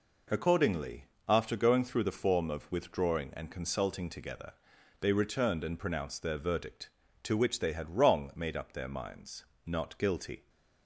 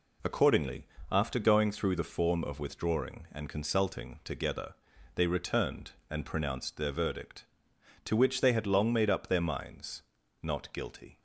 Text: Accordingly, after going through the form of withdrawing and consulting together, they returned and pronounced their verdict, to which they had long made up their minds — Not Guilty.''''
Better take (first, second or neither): second